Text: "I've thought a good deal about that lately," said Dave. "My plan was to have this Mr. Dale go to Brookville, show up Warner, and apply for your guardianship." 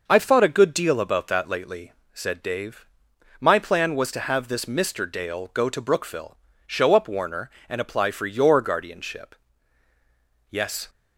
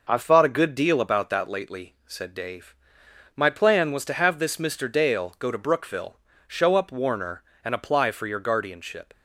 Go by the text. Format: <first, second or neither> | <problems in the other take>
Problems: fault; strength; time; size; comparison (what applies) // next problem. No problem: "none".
second | goes on to say "Yes"; slight; from 10.5 s on; 0.38 s long